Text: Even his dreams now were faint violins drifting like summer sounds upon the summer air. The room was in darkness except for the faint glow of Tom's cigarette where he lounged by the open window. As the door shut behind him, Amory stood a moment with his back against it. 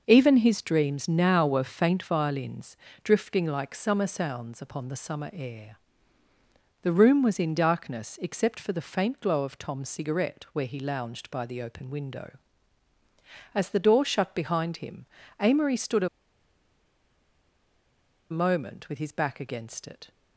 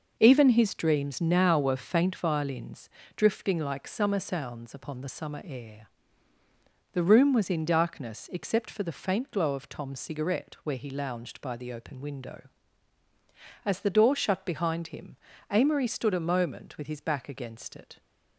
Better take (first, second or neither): second